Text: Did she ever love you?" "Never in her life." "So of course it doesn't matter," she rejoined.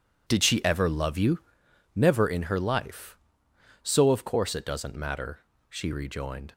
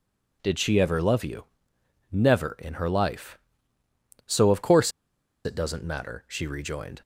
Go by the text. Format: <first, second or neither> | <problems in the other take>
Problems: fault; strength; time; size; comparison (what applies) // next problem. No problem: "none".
first | pauses between "course" and "it"; noticeable; at 4.8 s; 0.55 s long